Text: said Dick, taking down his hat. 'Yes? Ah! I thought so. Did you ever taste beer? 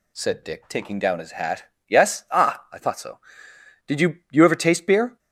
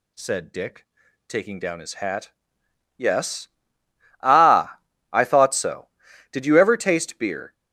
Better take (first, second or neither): second